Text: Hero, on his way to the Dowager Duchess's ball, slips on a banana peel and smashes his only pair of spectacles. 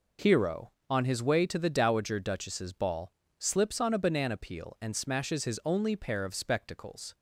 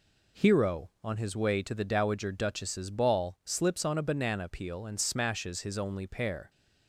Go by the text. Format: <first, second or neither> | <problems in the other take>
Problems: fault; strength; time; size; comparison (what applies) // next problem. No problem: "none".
first | stops before "of spectacles"; at 6.4 s